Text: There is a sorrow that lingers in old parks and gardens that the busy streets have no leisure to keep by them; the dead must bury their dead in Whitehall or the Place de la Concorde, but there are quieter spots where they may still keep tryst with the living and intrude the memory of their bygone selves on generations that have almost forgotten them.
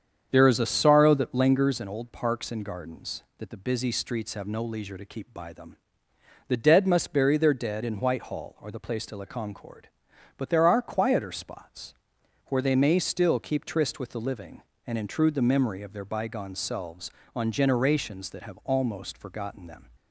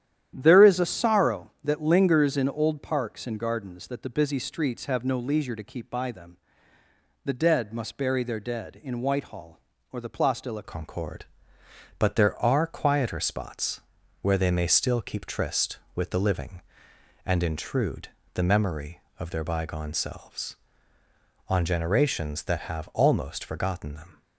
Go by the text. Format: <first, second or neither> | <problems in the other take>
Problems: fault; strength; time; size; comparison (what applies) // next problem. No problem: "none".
first | starts louder than the rest; strong; until 1.3 s; 10.5 dB; strong in the first // changes voice at "Concorde"; from 10.6 s on; 13.6 s long // pauses between "spots" and "where"; at 13.8 s; 0.40 s long; noticeable in the first // pauses between "intrude" and "the"; slight; at 18.0 s; 0.26 s long